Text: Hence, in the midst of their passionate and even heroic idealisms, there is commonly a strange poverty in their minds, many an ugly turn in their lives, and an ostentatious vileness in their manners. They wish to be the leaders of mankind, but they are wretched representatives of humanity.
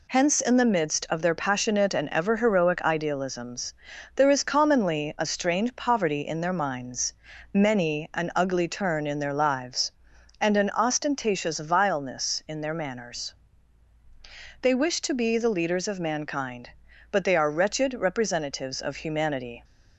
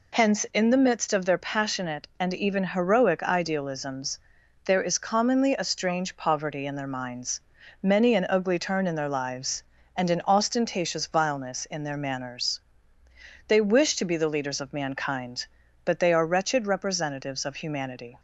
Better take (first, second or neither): second